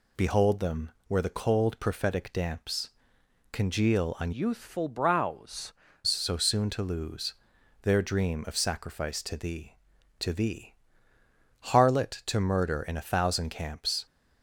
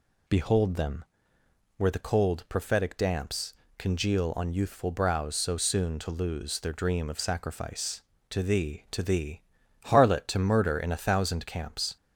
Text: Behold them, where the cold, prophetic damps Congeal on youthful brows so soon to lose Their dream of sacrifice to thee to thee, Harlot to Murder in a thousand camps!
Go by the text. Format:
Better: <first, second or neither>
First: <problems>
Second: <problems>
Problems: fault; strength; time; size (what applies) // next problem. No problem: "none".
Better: second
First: pauses between "damps" and "Congeal"; noticeable; at 2.9 s; 0.62 s long // changes voice from "youthful" to "brows"; from 4.3 to 5.7 s; 1.4 s long // pauses between "lose" and "Their"; noticeable; at 7.3 s; 0.50 s long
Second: pauses between "damps" and "Congeal"; slight; at 3.5 s; 0.26 s long